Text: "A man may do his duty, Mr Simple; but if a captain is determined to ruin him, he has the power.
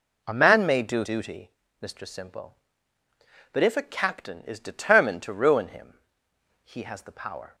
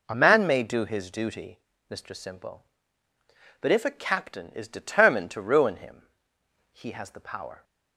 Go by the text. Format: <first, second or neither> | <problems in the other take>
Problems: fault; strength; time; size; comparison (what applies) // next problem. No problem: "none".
second | skips "his"; at 1.0 s